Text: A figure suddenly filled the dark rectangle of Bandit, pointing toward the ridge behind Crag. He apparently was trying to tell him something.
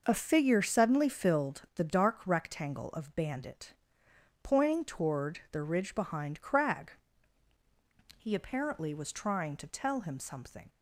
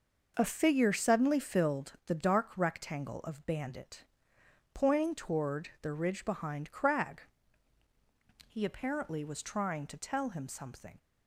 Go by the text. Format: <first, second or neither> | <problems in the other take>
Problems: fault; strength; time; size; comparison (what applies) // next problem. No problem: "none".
neither | none